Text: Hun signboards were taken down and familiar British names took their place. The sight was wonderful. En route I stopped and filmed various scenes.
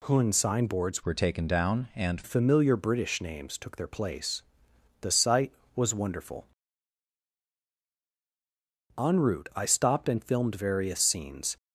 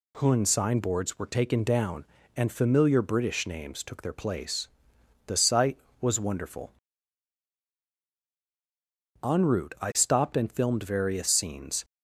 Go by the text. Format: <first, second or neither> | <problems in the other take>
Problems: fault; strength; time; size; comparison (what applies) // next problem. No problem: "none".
second | changes voice from "were" to "and"; from 1.0 to 2.2 s; 1.2 s long